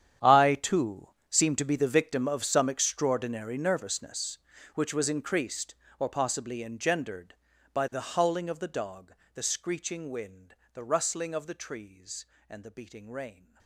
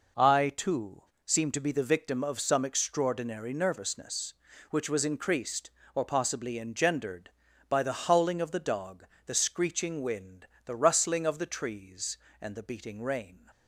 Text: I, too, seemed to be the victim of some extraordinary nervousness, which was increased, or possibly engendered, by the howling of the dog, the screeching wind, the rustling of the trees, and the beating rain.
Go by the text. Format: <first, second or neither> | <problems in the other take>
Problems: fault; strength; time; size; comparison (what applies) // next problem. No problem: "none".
second | gets quieter; strong; throughout; 18 dB